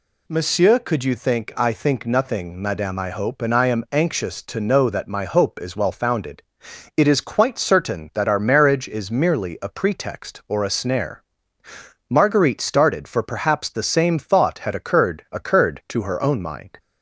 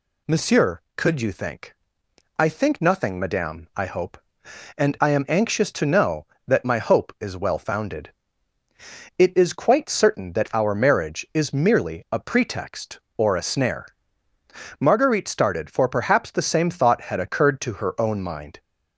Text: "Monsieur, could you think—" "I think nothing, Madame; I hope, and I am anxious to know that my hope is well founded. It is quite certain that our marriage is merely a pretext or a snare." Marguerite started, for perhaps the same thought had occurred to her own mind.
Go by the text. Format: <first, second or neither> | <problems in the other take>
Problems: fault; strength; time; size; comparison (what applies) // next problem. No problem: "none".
second | says "occurred" twice; at 15.3 s